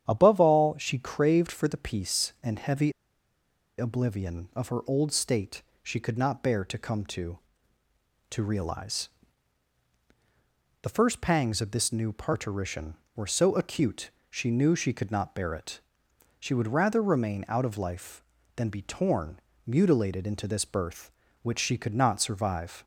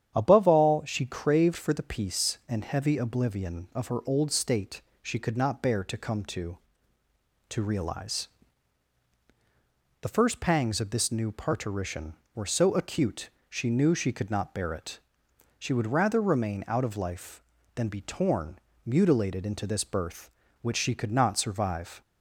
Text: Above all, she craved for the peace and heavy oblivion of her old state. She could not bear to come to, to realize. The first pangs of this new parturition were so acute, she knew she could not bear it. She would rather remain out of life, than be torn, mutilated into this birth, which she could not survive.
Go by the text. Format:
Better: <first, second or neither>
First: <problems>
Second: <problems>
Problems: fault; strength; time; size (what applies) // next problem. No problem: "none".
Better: second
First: starts louder than the rest; strong; until 1.1 s; 9.5 dB // pauses between "heavy" and "oblivion"; noticeable; at 2.9 s; 0.86 s long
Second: starts louder than the rest; strong; until 1.1 s; 9.5 dB